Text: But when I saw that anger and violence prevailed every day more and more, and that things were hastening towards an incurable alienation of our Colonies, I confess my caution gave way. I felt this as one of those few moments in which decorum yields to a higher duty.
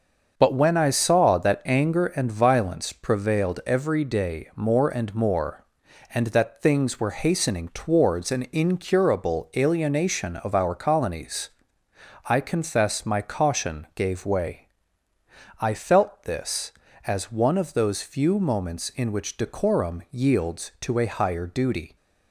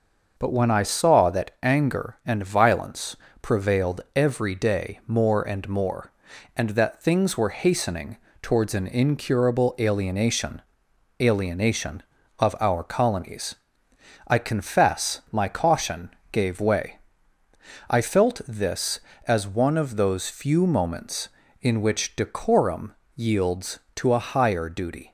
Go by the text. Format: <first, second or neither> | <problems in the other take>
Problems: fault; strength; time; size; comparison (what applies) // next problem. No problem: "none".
first | starts louder than the rest; noticeable; until 1.4 s; 6 dB; also in the first // pauses between "violence" and "prevailed"; slight; at 3.1 s; 0.26 s long // pauses between "hastening" and "towards"; slight; at 8.1 s; 0.24 s long // says "alienation" twice; at 11.1 s // pauses between "caution" and "gave"; slight; at 16.0 s; 0.20 s long // pauses between "decorum" and "yields"; slight; at 22.9 s; 0.22 s long